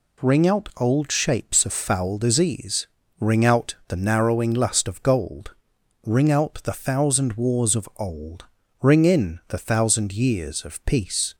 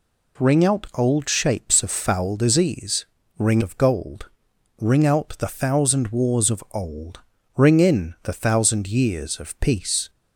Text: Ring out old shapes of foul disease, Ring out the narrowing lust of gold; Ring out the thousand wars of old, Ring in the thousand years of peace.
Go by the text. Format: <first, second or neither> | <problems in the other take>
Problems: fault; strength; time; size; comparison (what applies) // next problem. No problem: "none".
first | skips "out the narrowing lust"; at 3.6 s